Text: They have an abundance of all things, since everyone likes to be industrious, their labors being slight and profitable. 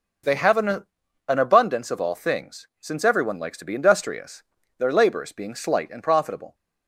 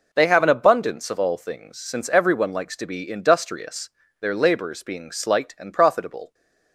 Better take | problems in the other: second | says "an" twice; at 1.2 s

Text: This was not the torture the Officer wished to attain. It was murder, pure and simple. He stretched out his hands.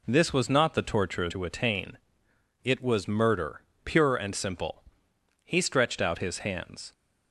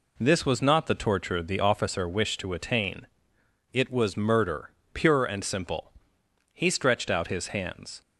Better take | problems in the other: second | skips "the Officer wished"; at 1.2 s

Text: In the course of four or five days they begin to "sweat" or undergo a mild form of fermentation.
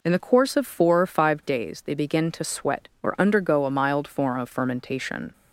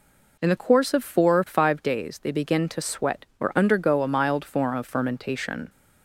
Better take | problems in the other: neither | none

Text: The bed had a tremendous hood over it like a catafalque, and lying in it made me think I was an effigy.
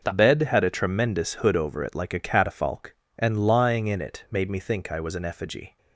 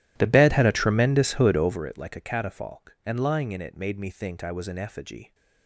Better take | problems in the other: first | starts louder than the rest; strong; until 2.0 s; 13.5 dB

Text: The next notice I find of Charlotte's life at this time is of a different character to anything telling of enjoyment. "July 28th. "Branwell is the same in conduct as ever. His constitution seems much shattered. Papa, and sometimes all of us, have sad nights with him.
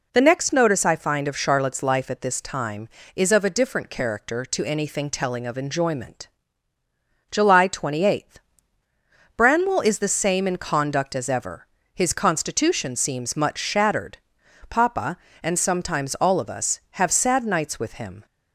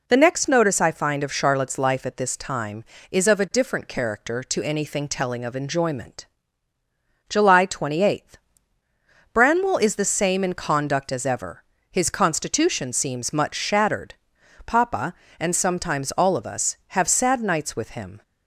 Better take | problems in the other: neither | none

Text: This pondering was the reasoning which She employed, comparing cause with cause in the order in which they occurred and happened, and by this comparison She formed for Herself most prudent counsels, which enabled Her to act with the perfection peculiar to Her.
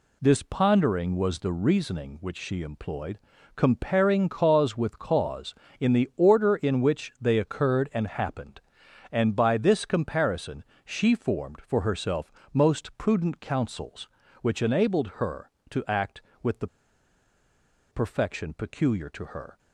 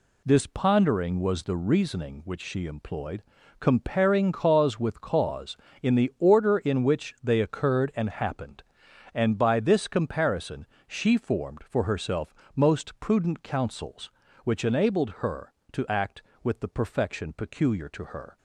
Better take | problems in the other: second | pauses between "comparison" and "She"; slight; at 10.6 s; 0.22 s long; slight in the second // pauses between "Herself" and "most"; slight; at 12.3 s; 0.22 s long; slight in the second // pauses between "the" and "perfection"; at 16.6 s; 1.2 s long

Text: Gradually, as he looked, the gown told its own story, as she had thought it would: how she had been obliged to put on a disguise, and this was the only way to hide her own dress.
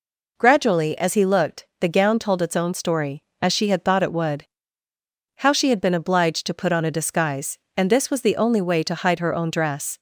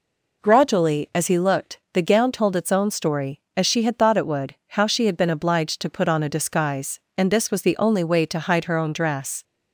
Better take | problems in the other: neither | none

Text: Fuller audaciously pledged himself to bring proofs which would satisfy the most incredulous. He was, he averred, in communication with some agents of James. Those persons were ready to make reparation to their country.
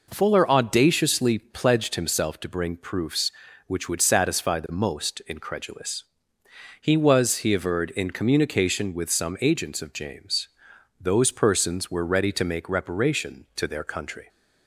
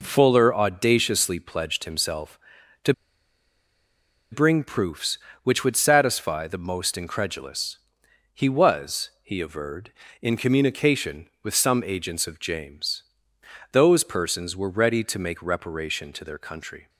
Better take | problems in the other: first | pauses between "to" and "bring"; strong; at 2.9 s; 1.3 s long

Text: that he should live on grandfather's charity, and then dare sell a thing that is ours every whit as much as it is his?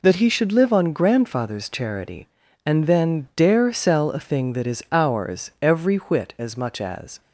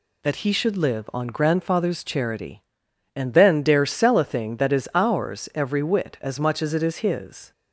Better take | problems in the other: second | stops before "it is his"; at 7.2 s

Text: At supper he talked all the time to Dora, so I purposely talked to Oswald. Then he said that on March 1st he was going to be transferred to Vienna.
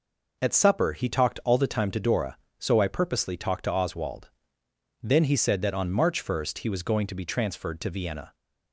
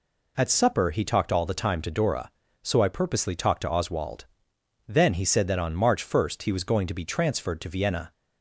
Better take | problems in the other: neither | none

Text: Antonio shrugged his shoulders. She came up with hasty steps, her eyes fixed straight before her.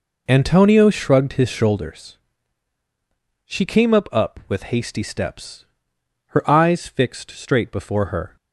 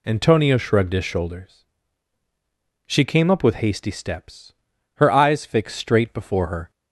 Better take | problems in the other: second | says "up" twice; at 4.1 s

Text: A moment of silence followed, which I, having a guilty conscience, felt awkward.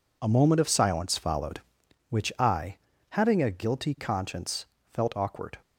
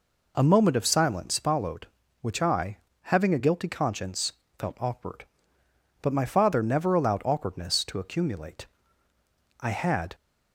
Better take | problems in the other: first | goes on to say "But my father never allowed awkwardness to accumulate I had"; strong; from 6.0 s on; 4.1 s long

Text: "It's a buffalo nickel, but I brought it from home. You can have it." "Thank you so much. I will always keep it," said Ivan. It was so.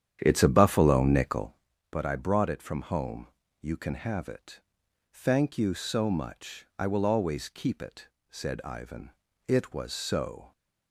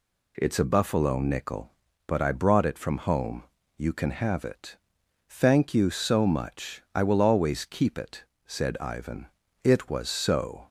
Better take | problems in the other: second | starts louder than the rest; strong; until 1.6 s; 9.5 dB

